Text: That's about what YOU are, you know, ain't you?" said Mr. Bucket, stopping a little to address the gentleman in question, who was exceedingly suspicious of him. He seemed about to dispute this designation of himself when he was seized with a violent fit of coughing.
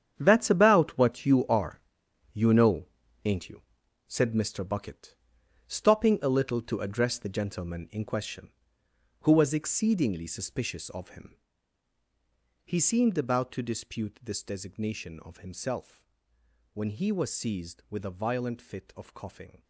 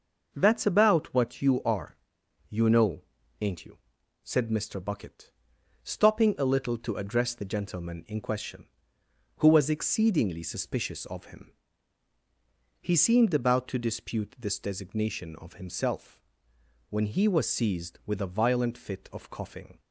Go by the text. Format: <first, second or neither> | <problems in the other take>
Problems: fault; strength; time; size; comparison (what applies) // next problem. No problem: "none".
second | gets quieter; strong; throughout; 12.5 dB // pauses between "himself" and "when"; noticeable; at 16.0 s; 0.66 s long; noticeable in the second